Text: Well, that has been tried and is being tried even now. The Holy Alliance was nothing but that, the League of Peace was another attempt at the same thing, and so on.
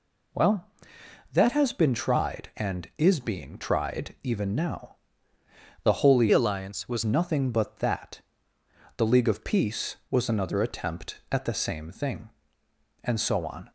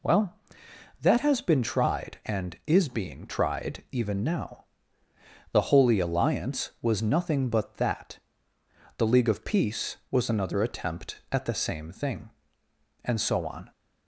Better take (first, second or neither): second